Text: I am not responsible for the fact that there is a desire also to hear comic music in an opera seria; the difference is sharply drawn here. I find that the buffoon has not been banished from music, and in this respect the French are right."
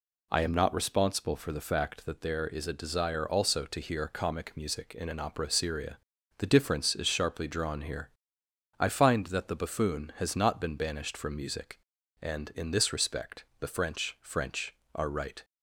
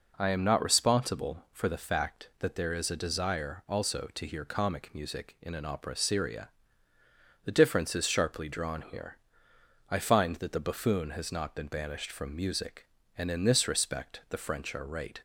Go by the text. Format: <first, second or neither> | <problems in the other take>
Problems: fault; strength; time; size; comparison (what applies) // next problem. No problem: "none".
second | pauses between "respect" and "the"; slight; at 13.4 s; 0.16 s long // says "French" twice; at 14.2 s